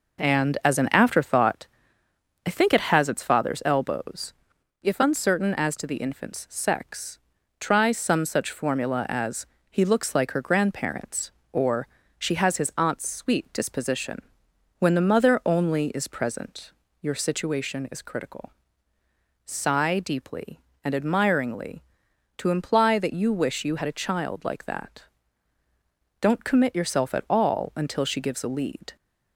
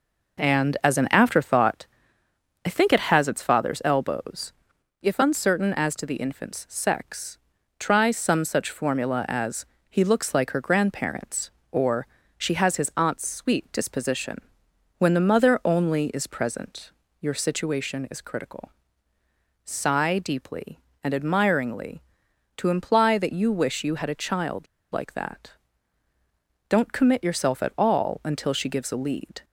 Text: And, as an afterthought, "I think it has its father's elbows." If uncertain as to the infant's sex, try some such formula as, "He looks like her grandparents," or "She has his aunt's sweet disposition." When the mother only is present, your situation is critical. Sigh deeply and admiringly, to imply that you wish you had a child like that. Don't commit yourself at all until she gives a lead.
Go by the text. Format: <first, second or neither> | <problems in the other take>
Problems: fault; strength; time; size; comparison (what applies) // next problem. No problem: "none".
first | pauses between "or" and "She"; slight; at 12.0 s; 0.30 s long; slight in the first // pauses between "child" and "like"; slight; at 24.6 s; 0.27 s long